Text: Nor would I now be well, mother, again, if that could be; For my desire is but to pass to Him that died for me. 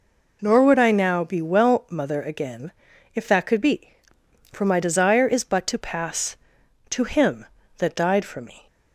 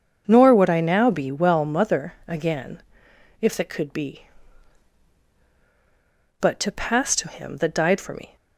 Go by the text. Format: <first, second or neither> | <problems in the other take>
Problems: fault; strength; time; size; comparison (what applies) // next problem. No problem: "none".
first | starts louder than the rest; until 1.2 s; 6.5 dB // skips "For my desire is"; at 5.3 s